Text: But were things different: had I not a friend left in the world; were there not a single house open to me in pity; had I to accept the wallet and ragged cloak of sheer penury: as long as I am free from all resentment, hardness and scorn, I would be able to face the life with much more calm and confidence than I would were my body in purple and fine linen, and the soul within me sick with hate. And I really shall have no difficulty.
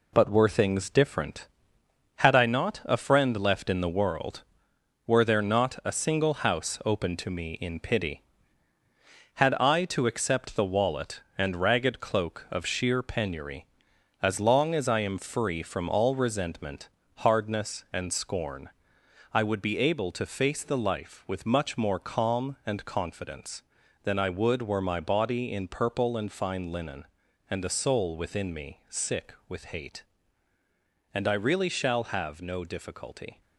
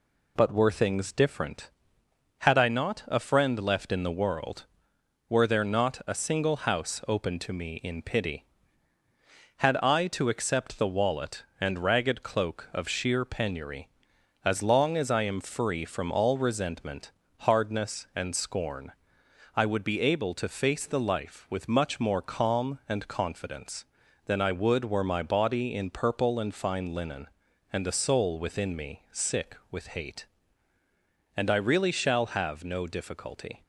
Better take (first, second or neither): second